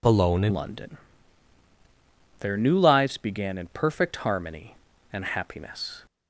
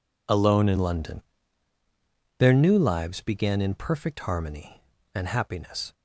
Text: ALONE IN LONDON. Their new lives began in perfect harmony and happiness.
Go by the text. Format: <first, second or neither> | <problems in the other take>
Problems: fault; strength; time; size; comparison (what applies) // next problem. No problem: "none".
second | changes voice at "LONDON"; from 0.5 s on; 5.5 s long